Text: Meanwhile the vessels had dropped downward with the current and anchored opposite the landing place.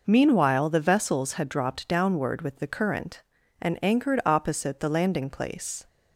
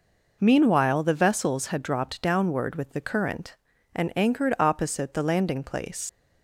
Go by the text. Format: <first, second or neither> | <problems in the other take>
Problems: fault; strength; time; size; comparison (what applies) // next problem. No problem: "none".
first | leaves "place" unfinished; at 6.0 s; 110 ms